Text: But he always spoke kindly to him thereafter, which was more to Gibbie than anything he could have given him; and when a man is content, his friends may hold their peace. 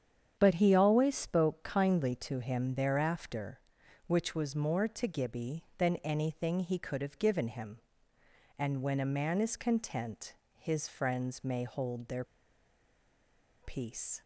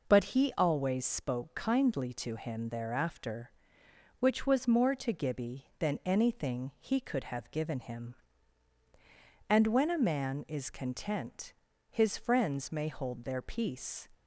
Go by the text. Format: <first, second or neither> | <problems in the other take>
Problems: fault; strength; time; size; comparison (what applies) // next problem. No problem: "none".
second | starts louder than the rest; strong; until 1.4 s; 8.5 dB // pauses between "their" and "peace"; strong; at 12.2 s; 1.3 s long